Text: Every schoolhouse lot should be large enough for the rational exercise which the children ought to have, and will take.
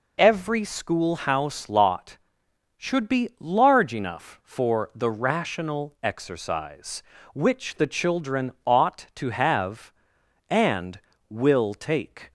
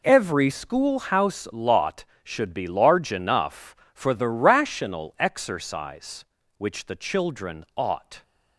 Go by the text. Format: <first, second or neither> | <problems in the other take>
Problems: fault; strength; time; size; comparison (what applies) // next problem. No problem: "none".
first | stops before "to have and will take"; at 8.2 s